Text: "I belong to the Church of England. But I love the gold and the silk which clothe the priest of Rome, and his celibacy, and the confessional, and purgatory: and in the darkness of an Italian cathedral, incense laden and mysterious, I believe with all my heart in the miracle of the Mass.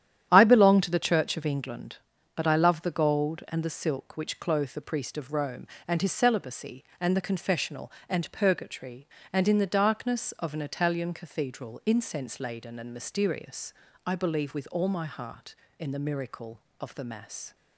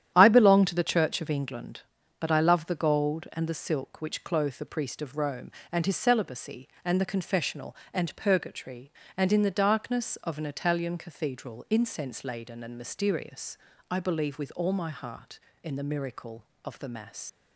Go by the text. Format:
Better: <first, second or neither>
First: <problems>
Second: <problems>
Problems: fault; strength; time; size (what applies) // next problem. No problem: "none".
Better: first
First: starts louder than the rest; strong; until 1.3 s; 10.5 dB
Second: starts louder than the rest; strong; until 1.1 s; 10.5 dB // leaves "Mass" unfinished; at 17.2 s; 95 ms